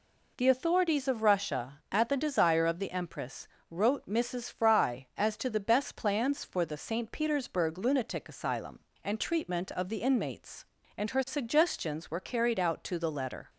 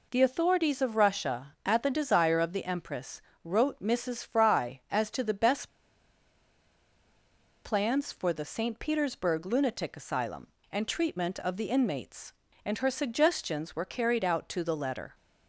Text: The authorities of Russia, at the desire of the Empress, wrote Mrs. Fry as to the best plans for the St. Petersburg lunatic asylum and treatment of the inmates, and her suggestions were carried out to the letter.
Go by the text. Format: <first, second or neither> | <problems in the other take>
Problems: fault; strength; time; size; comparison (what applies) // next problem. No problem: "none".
first | pauses between "best" and "plans"; strong; at 5.6 s; 1.9 s long